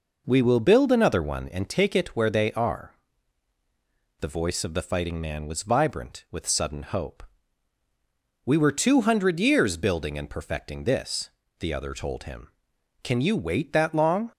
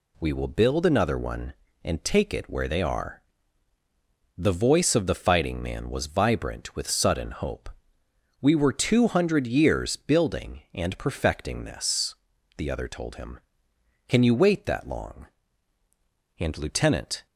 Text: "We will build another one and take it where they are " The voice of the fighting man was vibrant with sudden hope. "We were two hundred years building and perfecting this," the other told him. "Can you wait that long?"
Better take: first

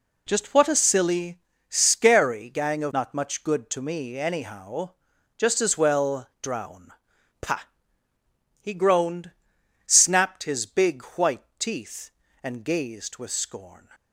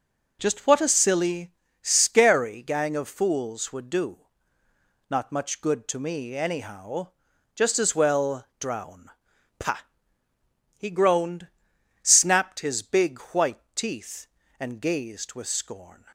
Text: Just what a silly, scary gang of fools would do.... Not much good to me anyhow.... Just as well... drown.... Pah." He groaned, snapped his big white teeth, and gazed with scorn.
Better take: second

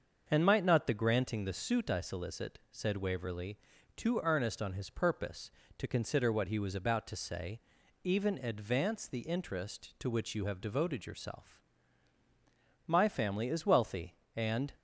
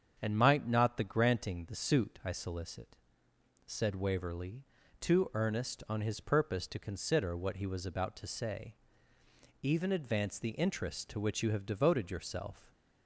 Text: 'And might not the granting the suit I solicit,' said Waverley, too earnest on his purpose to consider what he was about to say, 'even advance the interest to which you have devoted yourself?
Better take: second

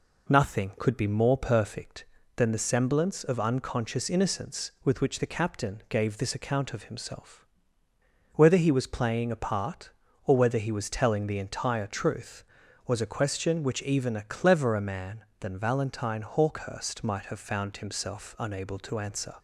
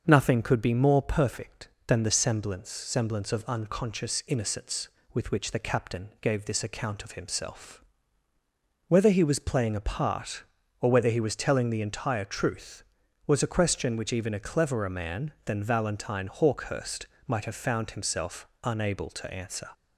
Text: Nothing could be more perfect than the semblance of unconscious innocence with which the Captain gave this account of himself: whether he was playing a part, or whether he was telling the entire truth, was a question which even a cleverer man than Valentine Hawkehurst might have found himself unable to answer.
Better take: first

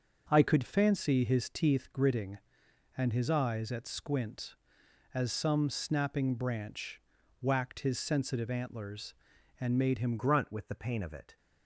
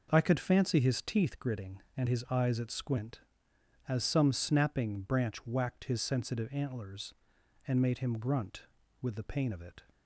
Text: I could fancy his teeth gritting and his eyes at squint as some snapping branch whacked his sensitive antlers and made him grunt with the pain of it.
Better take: second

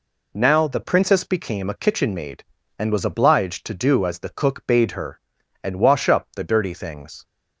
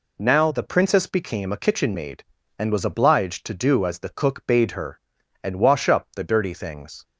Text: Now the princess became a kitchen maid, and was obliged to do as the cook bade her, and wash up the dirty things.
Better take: neither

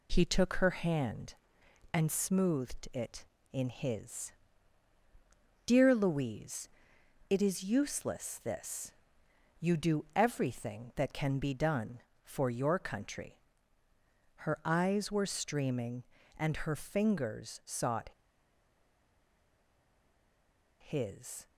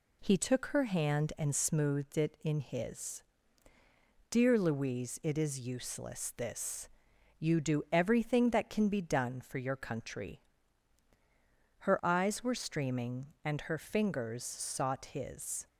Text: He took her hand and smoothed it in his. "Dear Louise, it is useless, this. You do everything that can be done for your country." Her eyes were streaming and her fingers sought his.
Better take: second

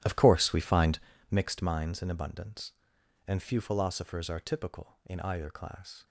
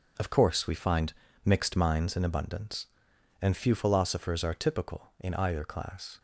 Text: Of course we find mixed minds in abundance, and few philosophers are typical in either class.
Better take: second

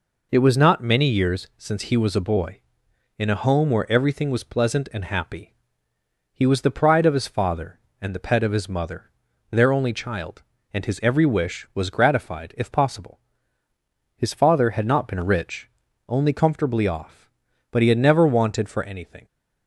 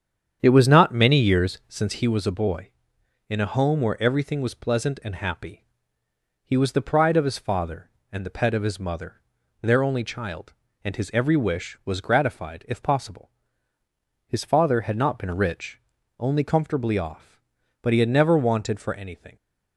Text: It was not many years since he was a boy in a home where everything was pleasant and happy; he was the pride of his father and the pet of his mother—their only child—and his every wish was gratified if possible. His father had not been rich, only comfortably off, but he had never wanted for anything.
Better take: first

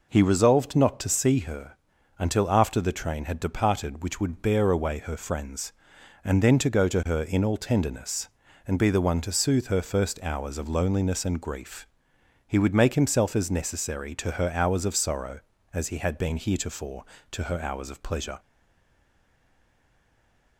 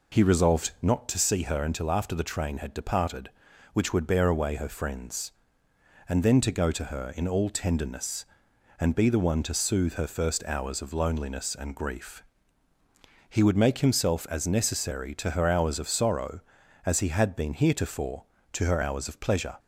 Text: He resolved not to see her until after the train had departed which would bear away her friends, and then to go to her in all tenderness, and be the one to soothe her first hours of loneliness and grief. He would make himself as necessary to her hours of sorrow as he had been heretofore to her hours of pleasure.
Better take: second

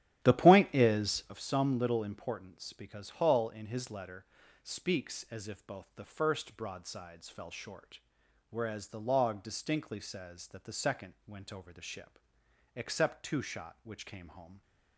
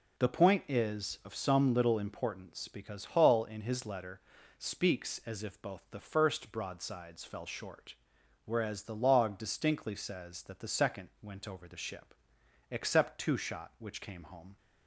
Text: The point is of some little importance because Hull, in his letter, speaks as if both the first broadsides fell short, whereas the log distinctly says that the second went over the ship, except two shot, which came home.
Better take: second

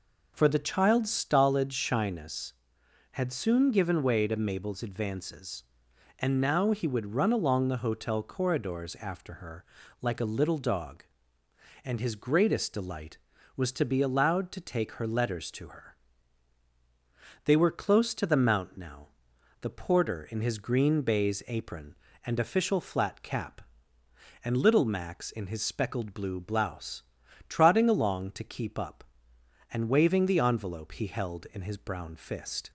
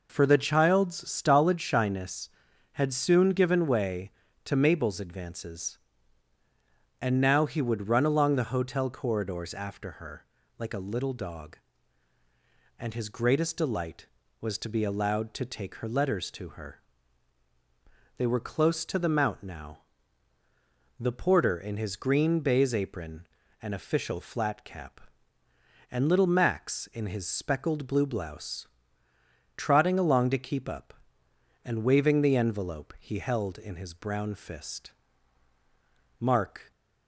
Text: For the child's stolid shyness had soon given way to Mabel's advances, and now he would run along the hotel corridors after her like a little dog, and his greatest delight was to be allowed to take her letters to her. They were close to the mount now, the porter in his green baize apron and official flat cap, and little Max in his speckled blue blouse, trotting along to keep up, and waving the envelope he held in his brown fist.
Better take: first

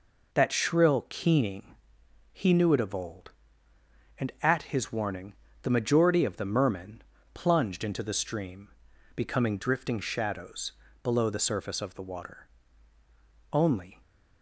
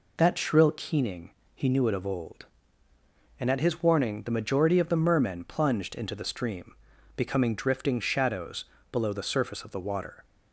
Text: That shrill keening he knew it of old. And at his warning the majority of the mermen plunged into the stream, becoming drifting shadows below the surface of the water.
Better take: second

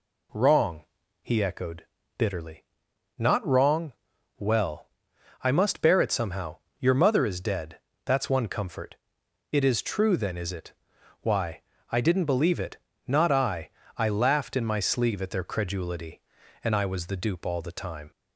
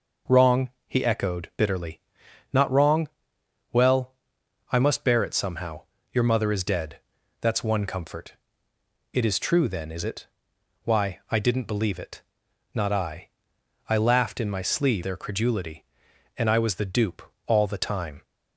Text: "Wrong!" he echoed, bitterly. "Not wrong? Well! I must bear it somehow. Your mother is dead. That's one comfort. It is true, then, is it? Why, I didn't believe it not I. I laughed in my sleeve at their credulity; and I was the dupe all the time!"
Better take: first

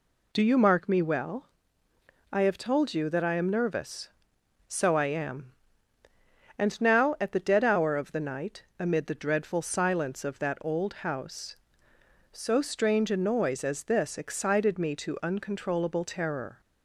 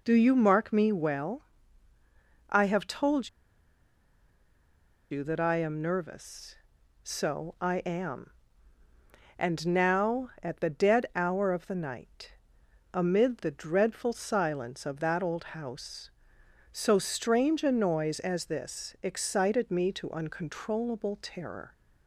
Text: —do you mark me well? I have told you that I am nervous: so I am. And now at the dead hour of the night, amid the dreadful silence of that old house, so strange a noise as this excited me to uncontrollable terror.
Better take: first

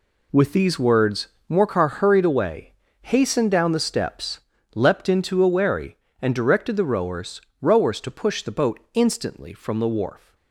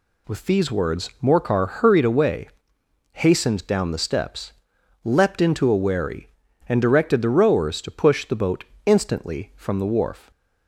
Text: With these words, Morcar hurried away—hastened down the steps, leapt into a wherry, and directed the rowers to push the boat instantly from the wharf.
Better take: second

